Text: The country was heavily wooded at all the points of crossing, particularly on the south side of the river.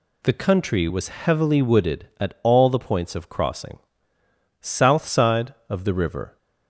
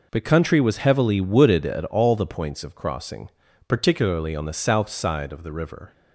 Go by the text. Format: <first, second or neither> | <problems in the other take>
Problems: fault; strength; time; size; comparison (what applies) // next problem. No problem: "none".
second | skips "particularly on the"; at 4.1 s